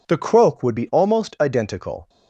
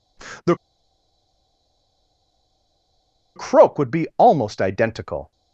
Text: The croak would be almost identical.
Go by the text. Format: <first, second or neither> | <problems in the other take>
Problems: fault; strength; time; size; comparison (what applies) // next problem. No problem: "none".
first | pauses between "The" and "croak"; strong; at 0.5 s; 2.8 s long